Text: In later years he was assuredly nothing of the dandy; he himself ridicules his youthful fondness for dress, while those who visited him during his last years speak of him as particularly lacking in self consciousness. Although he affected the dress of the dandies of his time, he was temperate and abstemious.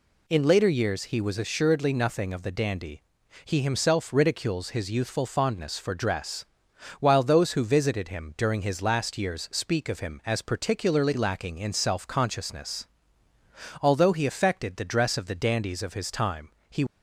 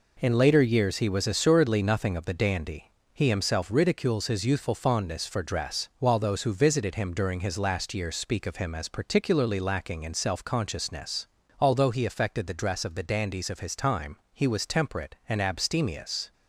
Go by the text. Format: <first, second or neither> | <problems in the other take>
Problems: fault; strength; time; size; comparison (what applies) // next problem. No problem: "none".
second | stops before "was temperate and abstemious"; at 16.8 s